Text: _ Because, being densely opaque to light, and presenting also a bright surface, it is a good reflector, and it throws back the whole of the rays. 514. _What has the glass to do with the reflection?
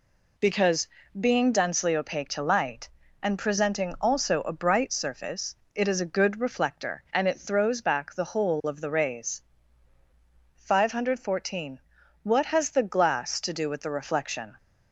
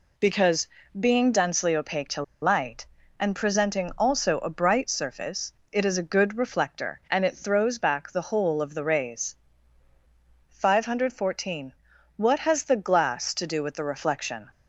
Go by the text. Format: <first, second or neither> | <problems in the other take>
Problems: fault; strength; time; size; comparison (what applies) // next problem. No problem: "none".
first | pauses between "to" and "light"; slight; at 2.2 s; 0.19 s long